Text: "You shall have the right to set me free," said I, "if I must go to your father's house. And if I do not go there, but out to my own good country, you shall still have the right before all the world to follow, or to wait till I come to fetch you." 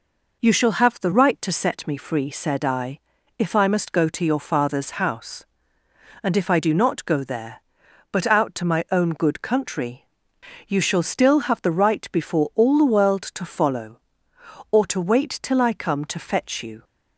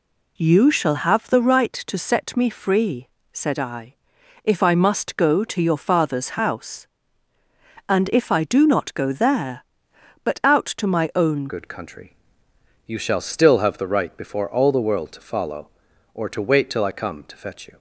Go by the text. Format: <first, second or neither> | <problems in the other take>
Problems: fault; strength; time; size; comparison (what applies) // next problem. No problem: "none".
first | changes voice at "good"; from 11.4 s on; 6.3 s long